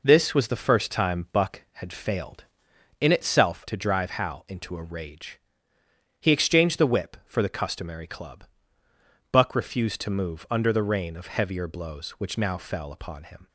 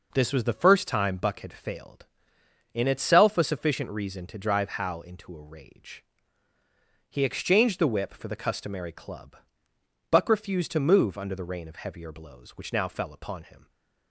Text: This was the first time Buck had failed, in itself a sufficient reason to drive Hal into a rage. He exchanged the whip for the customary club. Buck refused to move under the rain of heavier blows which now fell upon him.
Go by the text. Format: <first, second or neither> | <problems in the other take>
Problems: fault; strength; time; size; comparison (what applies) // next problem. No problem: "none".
second | skips "a sufficient reason"; at 3.6 s